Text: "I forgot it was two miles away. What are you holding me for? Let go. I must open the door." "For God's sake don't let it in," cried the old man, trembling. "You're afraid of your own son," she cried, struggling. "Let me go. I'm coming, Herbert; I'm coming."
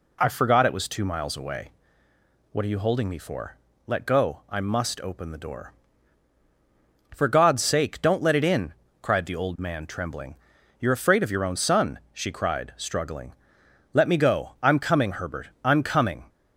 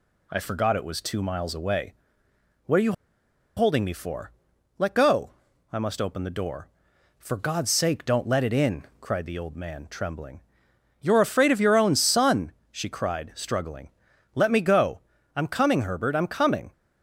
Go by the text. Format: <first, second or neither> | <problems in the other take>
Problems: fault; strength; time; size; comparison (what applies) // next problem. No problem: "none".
first | pauses between "you" and "holding"; noticeable; at 2.9 s; 0.64 s long